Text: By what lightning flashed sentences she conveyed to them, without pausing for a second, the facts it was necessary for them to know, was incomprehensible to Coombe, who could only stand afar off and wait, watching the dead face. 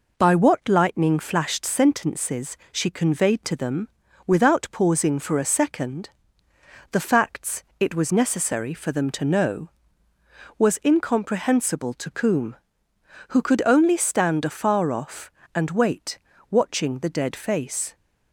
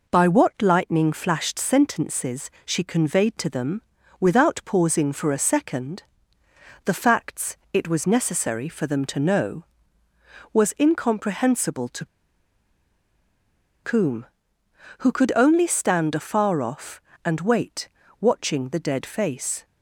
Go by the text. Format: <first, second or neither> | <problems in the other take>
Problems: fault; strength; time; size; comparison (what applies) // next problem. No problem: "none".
first | pauses between "sentences" and "she"; slight; at 2.4 s; 0.16 s long; slight in the first // pauses between "facts" and "it"; slight; at 7.5 s; 0.16 s long; slight in the first // pauses between "to" and "Coombe"; strong; at 12.0 s; 1.7 s long